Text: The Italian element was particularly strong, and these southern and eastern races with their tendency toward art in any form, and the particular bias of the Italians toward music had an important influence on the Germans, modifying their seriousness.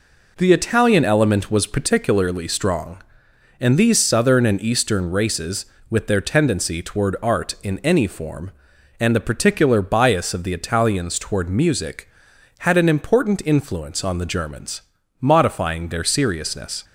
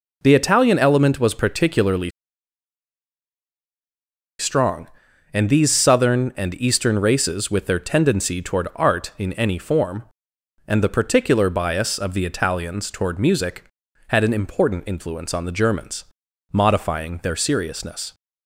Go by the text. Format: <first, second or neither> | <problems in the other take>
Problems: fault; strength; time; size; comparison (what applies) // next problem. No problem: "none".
first | pauses between "particularly" and "strong"; strong; at 2.1 s; 2.2 s long